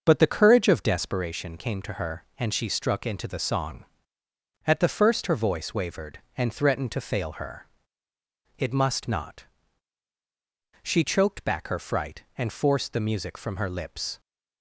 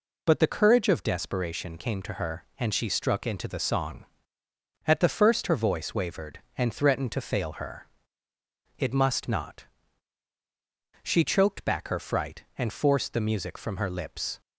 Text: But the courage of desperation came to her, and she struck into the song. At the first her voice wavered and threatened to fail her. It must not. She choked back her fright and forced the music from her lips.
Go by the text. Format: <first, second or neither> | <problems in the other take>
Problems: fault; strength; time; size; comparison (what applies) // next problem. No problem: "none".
second | starts louder than the rest; until 1.2 s; 6.5 dB